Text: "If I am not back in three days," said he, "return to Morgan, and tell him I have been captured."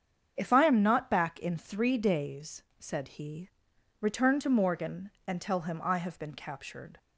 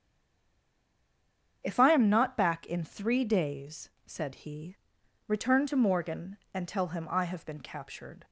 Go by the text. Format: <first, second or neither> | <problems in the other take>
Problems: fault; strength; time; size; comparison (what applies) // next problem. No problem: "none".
first | stays silent before the first word; noticeable; until 1.6 s; 1.6 s long // starts louder than the rest; strong; until 2.6 s; 7.5 dB; strong in the first